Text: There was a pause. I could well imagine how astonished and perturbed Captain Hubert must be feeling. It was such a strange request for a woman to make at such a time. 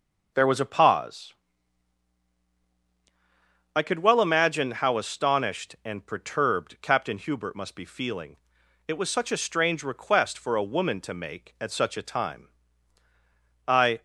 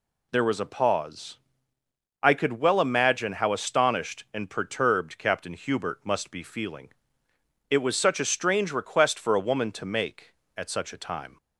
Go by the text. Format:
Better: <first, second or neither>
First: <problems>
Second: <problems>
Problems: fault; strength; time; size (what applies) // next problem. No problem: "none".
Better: second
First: goes on to say "I"; slight; from 13.6 s on; 0.36 s long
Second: none